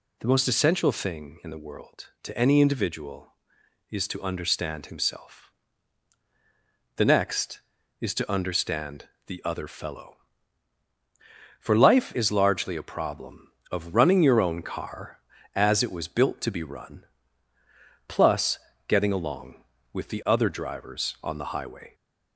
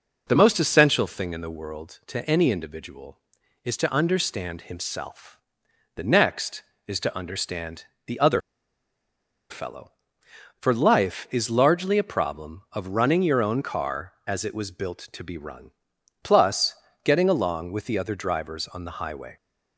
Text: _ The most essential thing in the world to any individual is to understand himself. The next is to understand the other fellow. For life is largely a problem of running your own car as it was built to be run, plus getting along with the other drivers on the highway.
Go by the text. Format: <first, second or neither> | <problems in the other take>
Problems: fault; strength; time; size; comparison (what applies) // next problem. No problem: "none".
first | pauses between "understand" and "the"; slight; at 7.8 s; 0.22 s long; slight in the first // pauses between "other" and "fellow"; at 8.4 s; 1.0 s long // pauses between "plus" and "getting"; slight; at 16.7 s; 0.30 s long; slight in the first